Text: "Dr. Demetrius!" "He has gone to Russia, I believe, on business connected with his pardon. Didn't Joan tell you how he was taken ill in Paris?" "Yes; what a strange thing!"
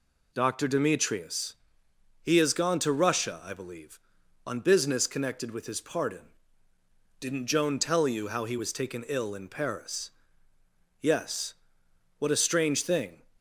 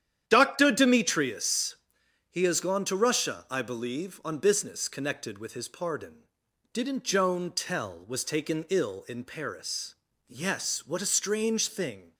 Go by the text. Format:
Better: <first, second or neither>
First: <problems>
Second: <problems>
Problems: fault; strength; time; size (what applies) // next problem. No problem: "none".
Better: first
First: none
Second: starts louder than the rest; strong; until 1.2 s; 10 dB // skips "you how he"; at 8.0 s